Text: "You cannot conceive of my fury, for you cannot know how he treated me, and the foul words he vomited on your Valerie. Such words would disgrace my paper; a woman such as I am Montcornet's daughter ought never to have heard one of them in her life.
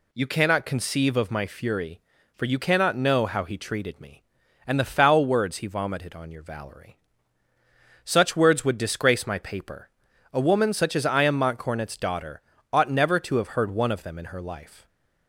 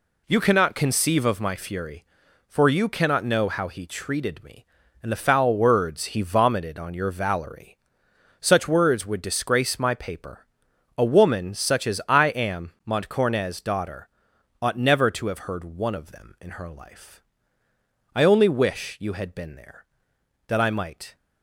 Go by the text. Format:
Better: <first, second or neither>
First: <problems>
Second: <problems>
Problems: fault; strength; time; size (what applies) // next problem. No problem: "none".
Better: first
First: pauses between "daughter" and "ought"; slight; at 12.4 s; 0.32 s long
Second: pauses between "daughter" and "ought"; noticeable; at 14.0 s; 0.54 s long // goes on to say "I only wish you had been there that I might"; strong; from 18.1 s on; 3.0 s long